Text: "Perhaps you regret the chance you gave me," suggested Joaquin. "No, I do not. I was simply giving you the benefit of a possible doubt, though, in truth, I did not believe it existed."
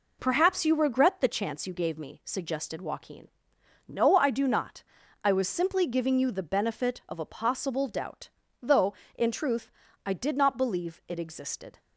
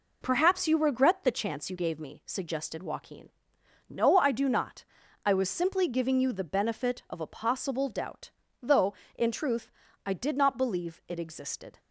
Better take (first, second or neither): neither